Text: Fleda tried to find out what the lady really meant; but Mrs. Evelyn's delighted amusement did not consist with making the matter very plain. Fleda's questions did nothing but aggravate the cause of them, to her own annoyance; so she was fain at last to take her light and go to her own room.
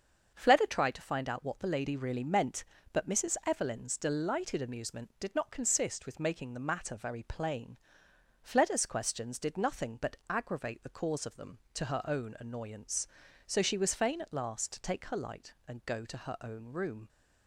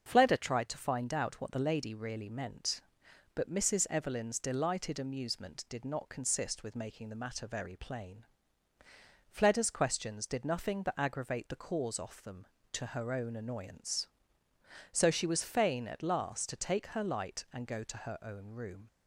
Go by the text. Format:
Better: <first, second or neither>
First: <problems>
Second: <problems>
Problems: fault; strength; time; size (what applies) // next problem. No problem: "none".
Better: first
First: starts louder than the rest; until 1.3 s; 7 dB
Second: starts louder than the rest; until 1.0 s; 7 dB // says "off" for "of"; at 11.9 s